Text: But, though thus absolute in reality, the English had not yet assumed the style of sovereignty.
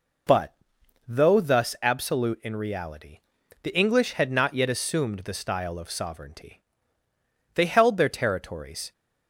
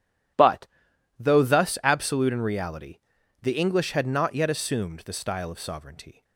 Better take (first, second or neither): second